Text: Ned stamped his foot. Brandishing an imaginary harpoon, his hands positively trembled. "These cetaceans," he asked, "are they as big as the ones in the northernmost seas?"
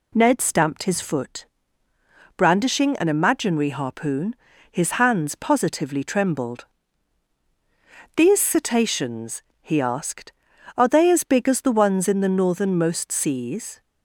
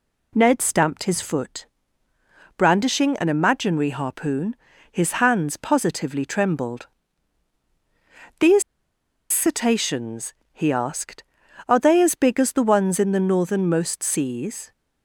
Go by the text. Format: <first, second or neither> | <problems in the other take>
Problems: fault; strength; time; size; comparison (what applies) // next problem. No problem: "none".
first | pauses between "These" and "cetaceans"; noticeable; at 8.6 s; 0.68 s long